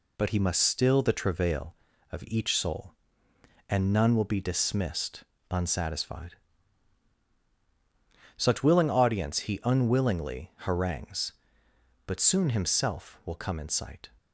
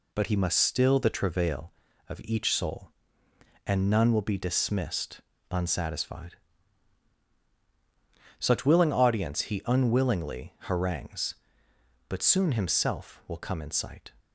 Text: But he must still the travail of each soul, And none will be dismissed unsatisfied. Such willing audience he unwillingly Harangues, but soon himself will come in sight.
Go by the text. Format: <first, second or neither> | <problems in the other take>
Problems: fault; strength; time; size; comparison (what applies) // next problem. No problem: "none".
neither | pauses between "dismissed" and "unsatisfied"; slight; the same in both